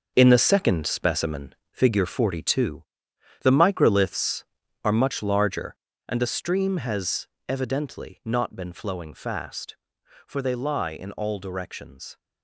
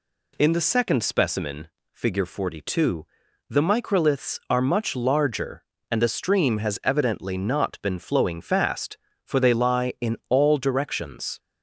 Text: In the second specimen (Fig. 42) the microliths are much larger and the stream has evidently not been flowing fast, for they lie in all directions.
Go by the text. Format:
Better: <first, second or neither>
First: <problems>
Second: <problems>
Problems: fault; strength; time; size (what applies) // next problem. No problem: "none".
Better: second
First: gets quieter; strong; throughout; 9.5 dB // pauses between "has" and "evidently"; slight; at 7.2 s; 0.20 s long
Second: none